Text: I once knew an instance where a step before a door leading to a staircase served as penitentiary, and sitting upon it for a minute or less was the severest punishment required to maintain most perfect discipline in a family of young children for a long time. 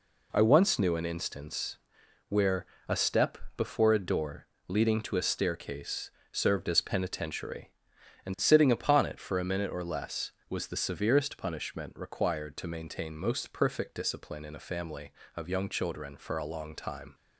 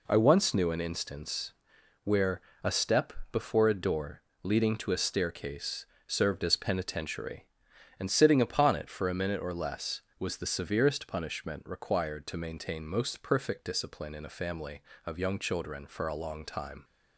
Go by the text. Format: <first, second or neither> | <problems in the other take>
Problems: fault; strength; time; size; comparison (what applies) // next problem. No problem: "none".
neither | pauses between "instance" and "where"; noticeable; the same in both // pauses between "where" and "a"; slight; the same in both // pauses between "step" and "before"; slight; the same in both // pauses between "door" and "leading"; slight; the same in both // pauses between "staircase" and "served"; slight; the same in both